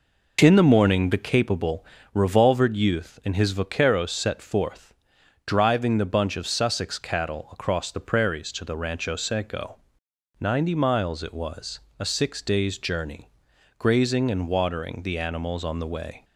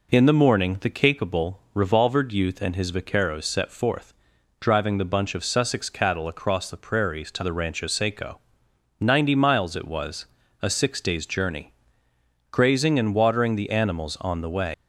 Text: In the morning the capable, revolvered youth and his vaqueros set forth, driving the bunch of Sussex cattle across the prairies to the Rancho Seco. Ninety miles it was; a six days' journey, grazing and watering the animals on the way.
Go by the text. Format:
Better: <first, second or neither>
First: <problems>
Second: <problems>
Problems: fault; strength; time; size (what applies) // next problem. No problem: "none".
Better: first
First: none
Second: leaves "way" unfinished; at 14.7 s; 105 ms